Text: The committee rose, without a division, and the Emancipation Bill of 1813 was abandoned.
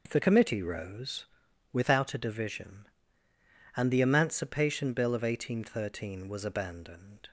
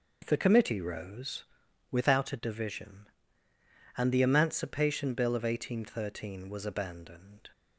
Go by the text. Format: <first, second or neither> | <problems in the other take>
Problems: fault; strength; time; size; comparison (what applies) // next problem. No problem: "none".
neither | none